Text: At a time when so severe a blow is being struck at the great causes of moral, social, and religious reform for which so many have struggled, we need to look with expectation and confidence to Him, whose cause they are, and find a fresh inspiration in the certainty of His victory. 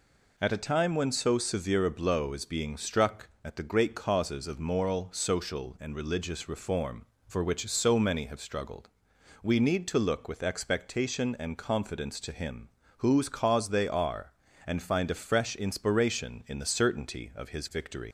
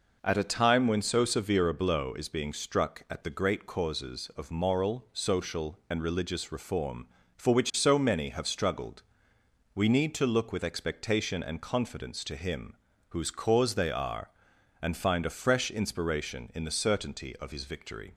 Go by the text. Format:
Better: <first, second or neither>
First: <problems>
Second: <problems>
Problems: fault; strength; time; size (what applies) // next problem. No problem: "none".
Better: second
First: leaves "victory" unfinished; at 18.0 s; 95 ms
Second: none